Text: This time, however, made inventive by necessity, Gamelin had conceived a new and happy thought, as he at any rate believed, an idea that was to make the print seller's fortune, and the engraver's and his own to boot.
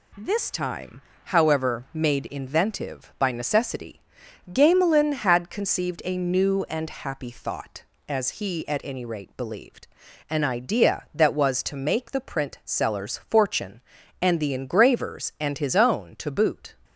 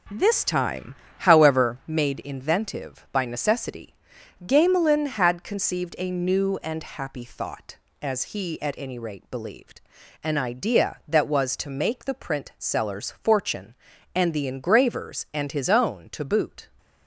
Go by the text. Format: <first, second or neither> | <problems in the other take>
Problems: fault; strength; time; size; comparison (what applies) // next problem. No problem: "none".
first | starts louder than the rest; until 1.8 s; 6 dB